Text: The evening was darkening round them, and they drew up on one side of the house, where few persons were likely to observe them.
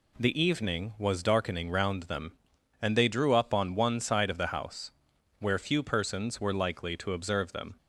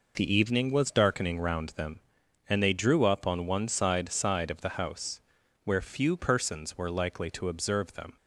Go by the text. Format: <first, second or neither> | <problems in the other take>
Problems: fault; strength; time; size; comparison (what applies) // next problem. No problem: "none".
first | says "side" twice; at 4.1 s